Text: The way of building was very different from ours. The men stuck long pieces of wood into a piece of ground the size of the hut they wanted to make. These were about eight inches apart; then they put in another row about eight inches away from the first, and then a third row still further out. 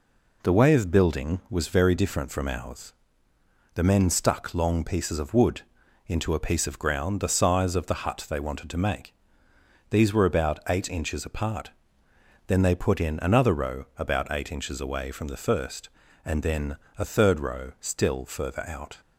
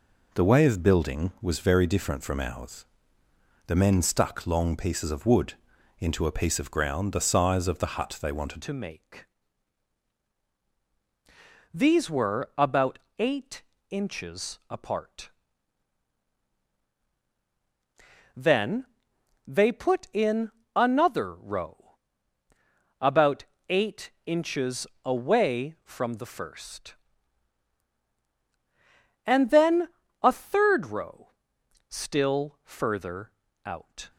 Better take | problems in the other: first | pauses between "wood" and "into"; noticeable; at 5.5 s; 0.46 s long; noticeable in the first // changes voice at "to"; from 8.6 s on; 25.4 s long // pauses between "about" and "eight"; slight; at 12.9 s; 0.20 s long // pauses between "eight" and "inches"; slight; at 13.6 s; 0.28 s long // pauses between "then" and "they"; noticeable; at 18.8 s; 0.60 s long // pauses between "in" and "another"; slight; at 20.4 s; 0.24 s long // pauses between "row" and "about"; at 21.9 s; 1.0 s long // pauses between "about" and "eight"; slight; at 23.4 s; 0.24 s long // pauses between "eight" and "inches"; slight; at 24.0 s; 0.16 s long // pauses between "inches" and "away"; slight; at 24.8 s; 0.18 s long // pauses between "then" and "a"; slight; at 29.8 s; 0.34 s long; slight in the first // pauses between "row" and "still"; noticeable; at 31.2 s; 0.62 s long // pauses between "further" and "out"; slight; at 33.2 s; 0.34 s long

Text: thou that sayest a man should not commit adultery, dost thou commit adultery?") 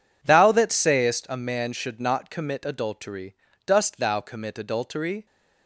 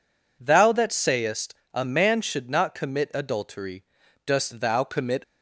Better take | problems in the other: first | pauses between "sayest" and "a"; slight; at 1.5 s; 0.18 s long // stops before "adultery"; at 5.2 s

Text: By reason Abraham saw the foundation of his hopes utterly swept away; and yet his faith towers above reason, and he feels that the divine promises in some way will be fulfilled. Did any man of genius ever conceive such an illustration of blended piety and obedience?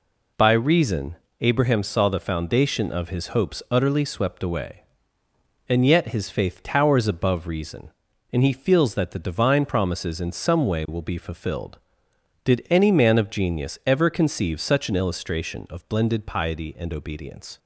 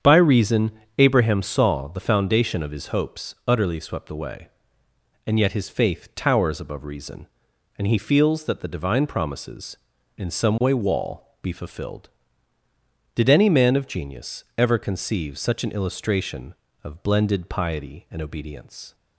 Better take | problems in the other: first | starts louder than the rest; strong; until 1.2 s; 8 dB // pauses between "reason" and "Abraham"; slight; at 0.7 s; 0.26 s long; slight in the first // says "wall" for "will"; at 10.7 s // pauses between "genius" and "ever"; slight; at 14.4 s; 0.16 s long

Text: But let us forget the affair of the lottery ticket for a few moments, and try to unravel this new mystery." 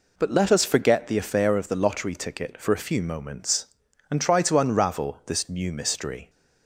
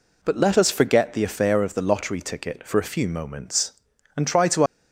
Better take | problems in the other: first | stops before "unravel this new mystery"; at 4.6 s

